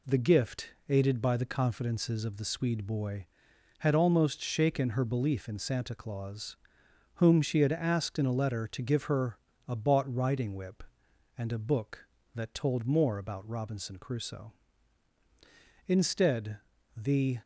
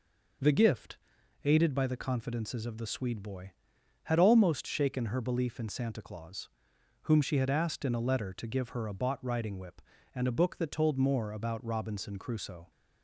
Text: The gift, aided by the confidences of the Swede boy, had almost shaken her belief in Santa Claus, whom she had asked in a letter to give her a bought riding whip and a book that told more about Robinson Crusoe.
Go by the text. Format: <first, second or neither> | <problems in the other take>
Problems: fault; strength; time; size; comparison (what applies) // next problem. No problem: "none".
second | pauses between "her" and "a"; slight; at 9.3 s; 0.28 s long // goes on to say "Instead the"; from 15.8 s on; 1.5 s long